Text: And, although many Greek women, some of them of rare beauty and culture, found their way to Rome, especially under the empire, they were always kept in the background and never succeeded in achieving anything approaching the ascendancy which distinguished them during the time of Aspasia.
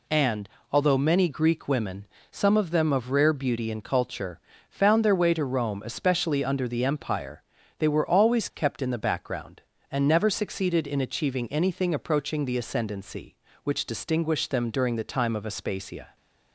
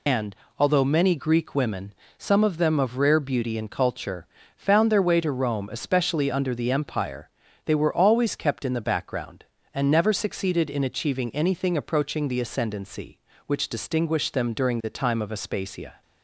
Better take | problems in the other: first | loses the start of "And"; at 0.0 s; 120 ms

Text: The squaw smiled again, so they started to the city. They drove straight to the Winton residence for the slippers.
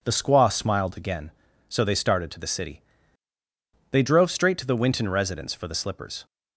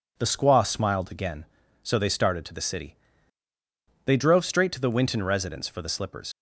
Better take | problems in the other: first | leaves "slippers" unfinished; at 6.3 s; 75 ms

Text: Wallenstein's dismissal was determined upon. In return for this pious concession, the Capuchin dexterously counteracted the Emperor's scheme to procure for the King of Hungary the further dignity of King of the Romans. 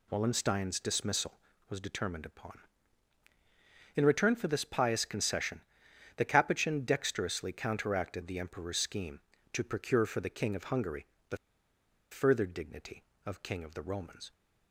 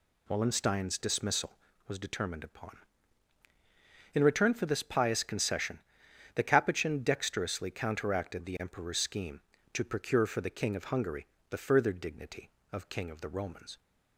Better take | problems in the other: second | pauses between "Hungary" and "the"; slight; at 11.0 s; 0.24 s long; slight in the second // pauses between "the" and "further"; noticeable; at 11.3 s; 0.75 s long

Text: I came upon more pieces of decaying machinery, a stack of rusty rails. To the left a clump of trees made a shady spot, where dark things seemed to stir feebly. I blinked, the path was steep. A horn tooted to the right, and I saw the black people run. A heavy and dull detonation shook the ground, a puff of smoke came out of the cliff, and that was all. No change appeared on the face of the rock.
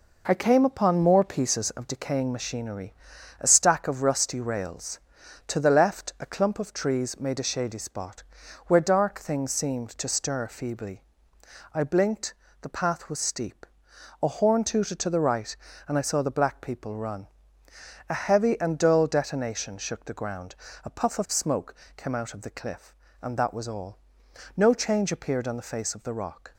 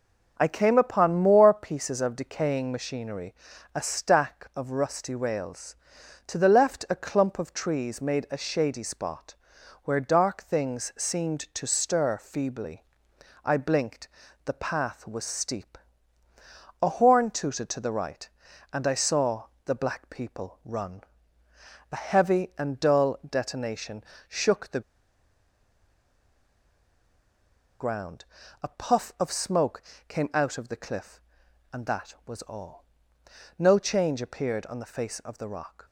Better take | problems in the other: first | pauses between "saw" and "the"; slight; at 19.4 s; 0.22 s long // pauses between "detonation" and "shook"; slight; at 24.0 s; 0.26 s long // pauses between "the" and "ground"; strong; at 24.8 s; 2.9 s long // pauses between "smoke" and "came"; slight; at 29.8 s; 0.24 s long; slight in the first

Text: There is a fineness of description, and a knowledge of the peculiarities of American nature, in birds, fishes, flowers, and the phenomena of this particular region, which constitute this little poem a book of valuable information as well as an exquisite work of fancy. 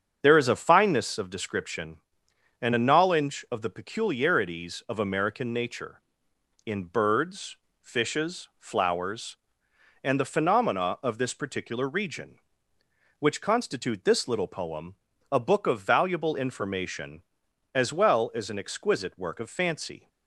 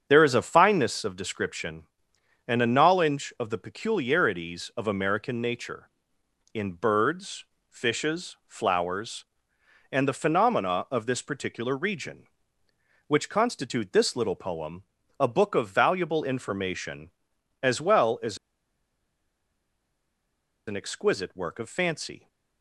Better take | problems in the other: first | starts louder than the rest; strong; until 1.1 s; 7 dB; strong in the first // pauses between "poem" and "a"; slight; at 14.8 s; 0.36 s long; slight in the first // pauses between "as" and "an"; strong; at 18.3 s; 2.3 s long

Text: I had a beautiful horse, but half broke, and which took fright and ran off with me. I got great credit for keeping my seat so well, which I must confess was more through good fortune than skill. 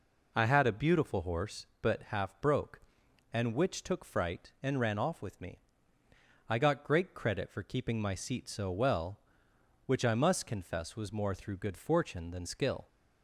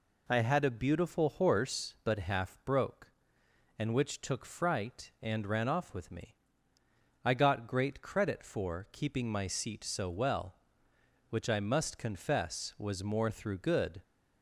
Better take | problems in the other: first | stops before "fortune than skill"; at 14.0 s

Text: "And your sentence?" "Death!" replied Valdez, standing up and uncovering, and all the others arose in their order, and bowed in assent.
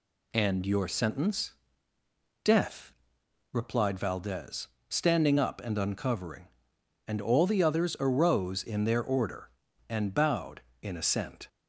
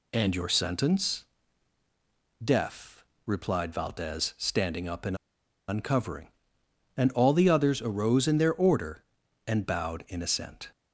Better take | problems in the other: first | pauses between "and" and "uncovering"; noticeable; at 5.1 s; 0.53 s long

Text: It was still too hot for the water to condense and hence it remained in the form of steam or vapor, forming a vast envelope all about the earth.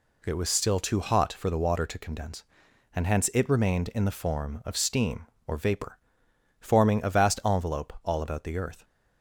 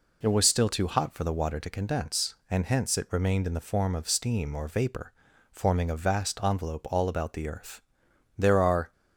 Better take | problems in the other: first | goes on to say "There are"; from 8.3 s on; 0.54 s long

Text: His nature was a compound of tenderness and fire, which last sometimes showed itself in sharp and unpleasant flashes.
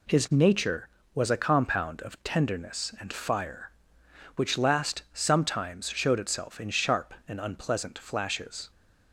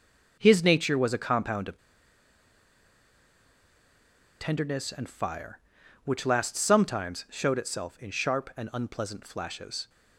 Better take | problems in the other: first | pauses between "of" and "tenderness"; strong; at 1.7 s; 2.6 s long

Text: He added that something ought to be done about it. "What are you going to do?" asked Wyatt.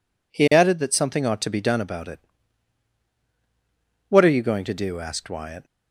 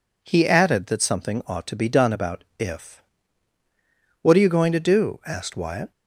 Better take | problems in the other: first | says "if" for "it"; at 2.5 s

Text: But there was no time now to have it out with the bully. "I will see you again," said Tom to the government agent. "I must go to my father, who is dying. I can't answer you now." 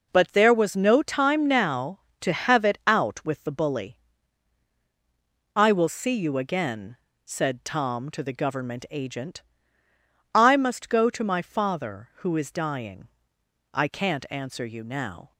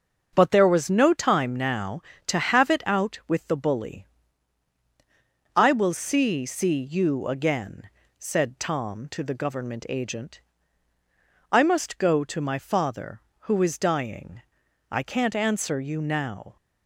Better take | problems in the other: first | starts louder than the rest; until 1.3 s; 6.5 dB // says "see" twice; at 6.4 s

